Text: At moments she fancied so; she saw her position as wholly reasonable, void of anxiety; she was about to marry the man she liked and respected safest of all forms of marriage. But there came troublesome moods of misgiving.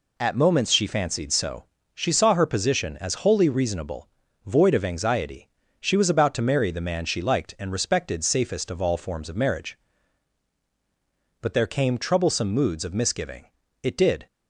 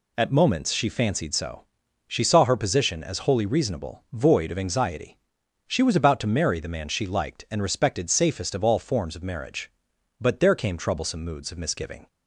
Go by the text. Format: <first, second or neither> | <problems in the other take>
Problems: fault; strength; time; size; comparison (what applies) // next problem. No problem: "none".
second | goes on to say "It did"; slight; from 13.8 s on; 0.44 s long